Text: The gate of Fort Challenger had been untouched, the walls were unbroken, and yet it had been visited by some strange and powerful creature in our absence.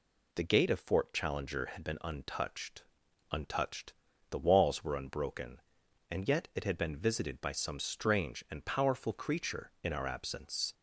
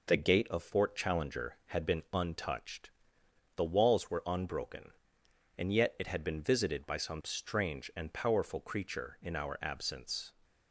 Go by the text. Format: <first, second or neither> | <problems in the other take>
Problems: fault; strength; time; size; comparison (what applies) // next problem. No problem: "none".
second | says "untouched" twice; at 3.3 s